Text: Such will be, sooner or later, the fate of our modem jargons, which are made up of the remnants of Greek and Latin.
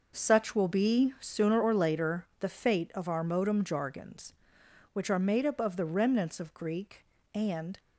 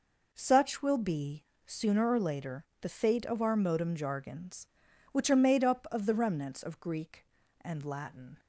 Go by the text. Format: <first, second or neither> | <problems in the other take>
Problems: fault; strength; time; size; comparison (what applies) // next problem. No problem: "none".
second | stops before "Latin"; at 7.7 s